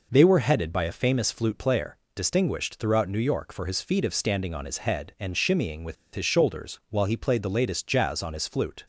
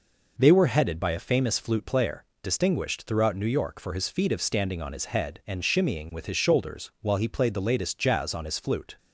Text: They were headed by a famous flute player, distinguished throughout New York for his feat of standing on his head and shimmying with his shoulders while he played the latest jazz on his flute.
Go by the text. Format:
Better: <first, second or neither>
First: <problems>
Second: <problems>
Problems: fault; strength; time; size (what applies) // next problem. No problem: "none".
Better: second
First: pauses between "with" and "his"; slight; at 5.9 s; 0.20 s long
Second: none